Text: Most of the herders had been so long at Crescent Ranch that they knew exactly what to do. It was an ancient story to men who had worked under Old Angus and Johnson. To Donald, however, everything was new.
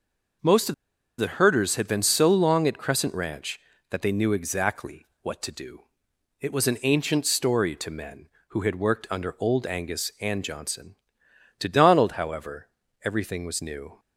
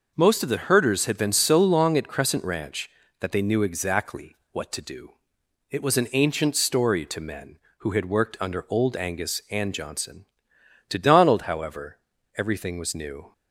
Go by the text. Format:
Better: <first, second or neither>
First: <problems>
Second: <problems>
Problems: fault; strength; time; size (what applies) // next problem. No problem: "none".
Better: second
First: pauses between "of" and "the"; at 0.7 s; 0.44 s long // pauses between "exactly" and "what"; slight; at 5.0 s; 0.16 s long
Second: pauses between "exactly" and "what"; slight; at 4.3 s; 0.16 s long